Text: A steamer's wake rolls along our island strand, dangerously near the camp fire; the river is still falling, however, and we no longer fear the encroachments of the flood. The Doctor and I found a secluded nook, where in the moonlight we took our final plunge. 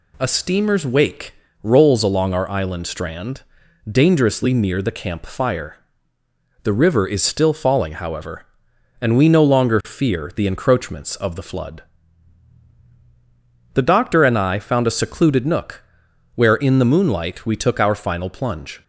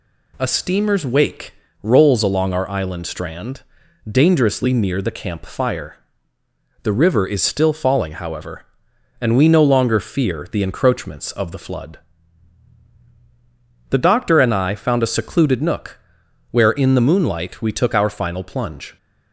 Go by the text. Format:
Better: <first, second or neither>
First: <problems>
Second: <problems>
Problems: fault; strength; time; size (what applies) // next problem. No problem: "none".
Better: neither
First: pauses between "wake" and "rolls"; slight; at 1.3 s; 0.28 s long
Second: pauses between "wake" and "rolls"; slight; at 1.5 s; 0.28 s long